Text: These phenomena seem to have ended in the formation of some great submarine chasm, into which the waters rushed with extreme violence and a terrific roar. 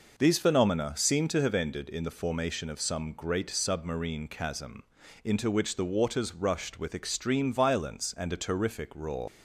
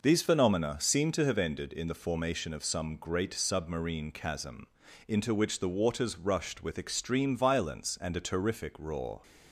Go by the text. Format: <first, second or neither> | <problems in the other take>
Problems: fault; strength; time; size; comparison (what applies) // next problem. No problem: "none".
second | leaves "roar" unfinished; at 9.2 s; 110 ms